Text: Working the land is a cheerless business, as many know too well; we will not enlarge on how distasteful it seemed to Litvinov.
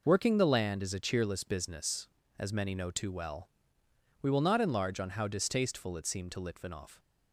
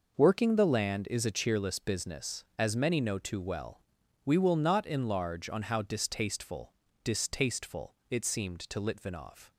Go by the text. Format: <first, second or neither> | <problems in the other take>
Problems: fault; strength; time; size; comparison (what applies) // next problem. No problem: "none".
first | says "distasteful" twice; at 7.0 s